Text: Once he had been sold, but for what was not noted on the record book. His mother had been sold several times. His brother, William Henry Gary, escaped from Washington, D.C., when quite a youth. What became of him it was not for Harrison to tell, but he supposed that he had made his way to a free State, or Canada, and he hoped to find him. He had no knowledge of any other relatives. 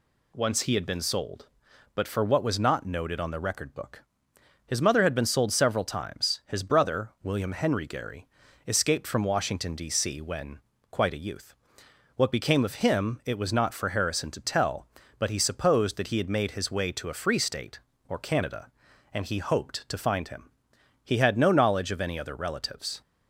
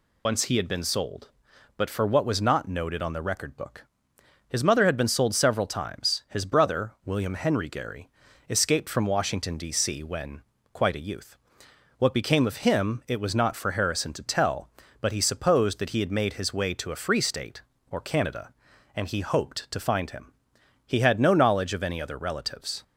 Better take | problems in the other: first | loses the start of "Once"; at 0.2 s; 85 ms // pauses between "when" and "quite"; slight; at 10.4 s; 0.32 s long; slight in the first

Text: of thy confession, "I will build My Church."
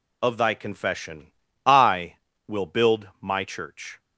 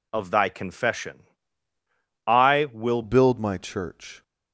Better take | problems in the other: first | changes voice at "build"; from 3.0 s on; 1.2 s long

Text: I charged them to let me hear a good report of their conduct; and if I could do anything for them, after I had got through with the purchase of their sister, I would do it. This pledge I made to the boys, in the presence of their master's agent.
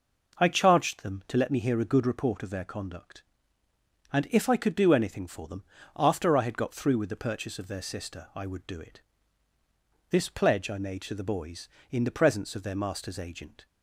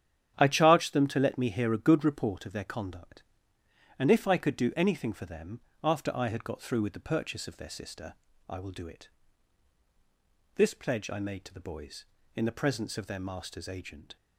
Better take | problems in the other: first | starts louder than the rest; strong; until 1.3 s; 10 dB // says "will" for "would"; at 8.5 s

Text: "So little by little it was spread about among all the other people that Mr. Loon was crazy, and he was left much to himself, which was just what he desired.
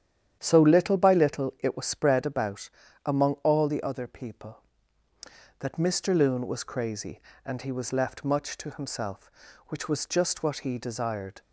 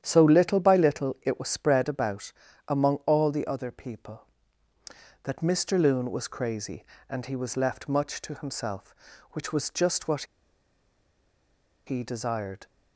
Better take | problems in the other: first | starts louder than the rest; strong; until 1.0 s; 9.5 dB; strong in the first // pauses between "about" and "among"; slight; at 2.3 s; 0.34 s long; slight in the first // pauses between "what" and "he"; strong; at 10.2 s; 1.6 s long

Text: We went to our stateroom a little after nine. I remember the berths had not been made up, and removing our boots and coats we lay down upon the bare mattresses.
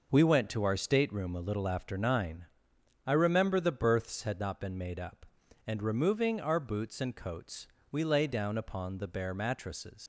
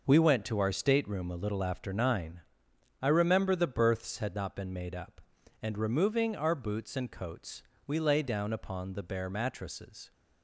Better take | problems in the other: second | pauses between "coats" and "we"; slight; at 7.6 s; 0.24 s long; slight in the second // leaves "mattresses" unfinished; at 10.0 s; 105 ms

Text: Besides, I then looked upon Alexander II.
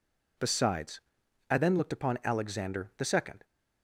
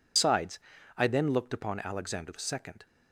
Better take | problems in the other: first | loses the start of "Besides"; at 0.1 s; 110 ms

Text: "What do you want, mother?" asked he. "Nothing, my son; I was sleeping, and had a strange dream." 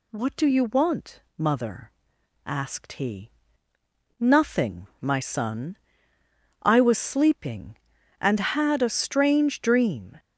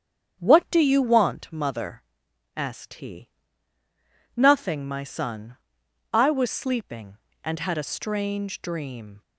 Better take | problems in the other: first | starts louder than the rest; strong; until 1.5 s; 8.5 dB

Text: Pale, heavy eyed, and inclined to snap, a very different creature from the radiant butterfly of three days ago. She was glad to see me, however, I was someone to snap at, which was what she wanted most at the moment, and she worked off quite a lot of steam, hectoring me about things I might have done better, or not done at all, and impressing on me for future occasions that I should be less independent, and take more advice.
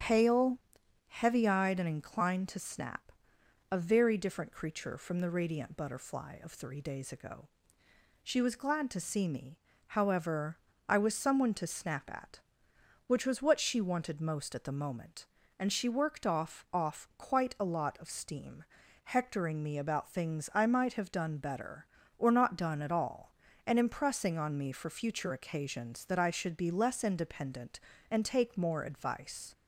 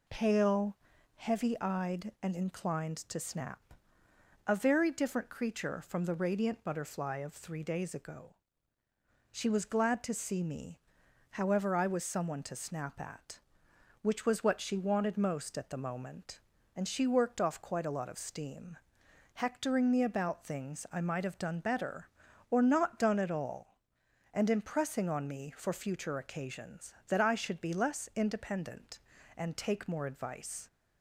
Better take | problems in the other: second | starts louder than the rest; strong; until 1.5 s; 8.5 dB // says "off" twice; at 16.7 s

